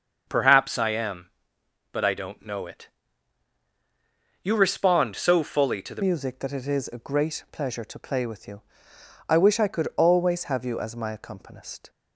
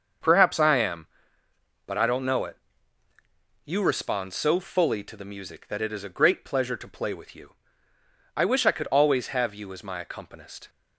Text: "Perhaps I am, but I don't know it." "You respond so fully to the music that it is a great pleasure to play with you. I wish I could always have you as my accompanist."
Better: second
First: starts louder than the rest; until 1.2 s; 6.5 dB // changes voice at "music"; from 6.0 s on; 5.8 s long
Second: starts louder than the rest; until 1.9 s; 6.5 dB

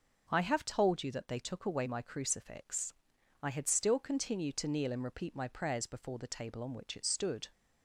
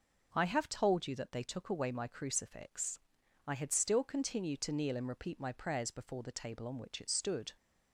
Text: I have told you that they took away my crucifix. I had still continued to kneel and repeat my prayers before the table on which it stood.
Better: neither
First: none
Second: none

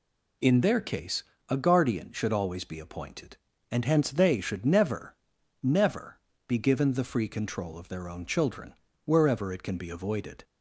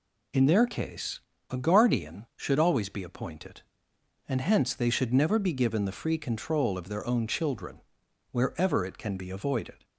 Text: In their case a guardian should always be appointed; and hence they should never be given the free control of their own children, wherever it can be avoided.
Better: second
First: pauses between "case" and "a"; slight; at 1.2 s; 0.24 s long // says "never" twice; at 5.6 s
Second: pauses between "case" and "a"; slight; at 1.2 s; 0.30 s long

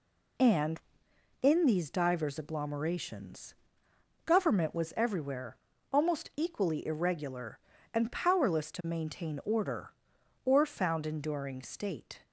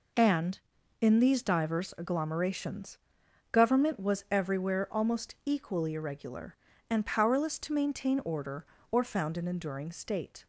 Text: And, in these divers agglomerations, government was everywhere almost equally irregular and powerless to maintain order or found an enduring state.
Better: second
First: pauses between "everywhere" and "almost"; slight; at 5.5 s; 0.34 s long // skips "an"; at 11.0 s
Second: none

